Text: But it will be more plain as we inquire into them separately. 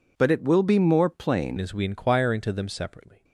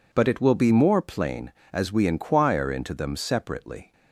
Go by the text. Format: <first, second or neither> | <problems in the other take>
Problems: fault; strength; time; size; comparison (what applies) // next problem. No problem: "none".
second | changes voice at "as"; from 1.5 s on; 1.7 s long